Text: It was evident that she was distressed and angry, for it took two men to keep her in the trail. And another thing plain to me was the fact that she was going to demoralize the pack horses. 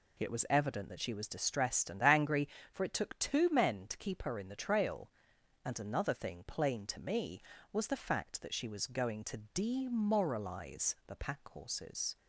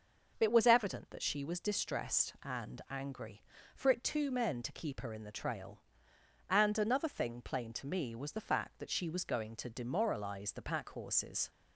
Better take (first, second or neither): first